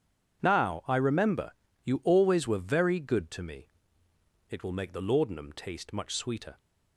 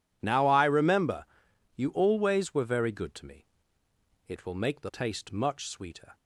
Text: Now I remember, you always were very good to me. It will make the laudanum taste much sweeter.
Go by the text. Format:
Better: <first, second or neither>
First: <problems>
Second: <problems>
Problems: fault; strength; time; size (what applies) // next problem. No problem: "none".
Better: first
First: none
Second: skips "laudanum"; at 4.9 s